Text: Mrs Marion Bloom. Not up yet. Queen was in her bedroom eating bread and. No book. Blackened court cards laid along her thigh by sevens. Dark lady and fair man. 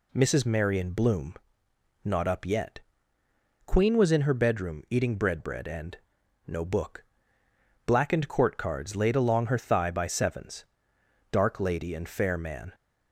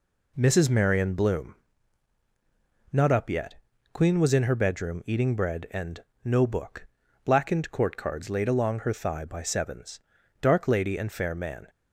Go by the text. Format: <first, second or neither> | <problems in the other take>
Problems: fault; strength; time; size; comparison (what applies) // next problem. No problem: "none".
second | says "bread" twice; at 5.4 s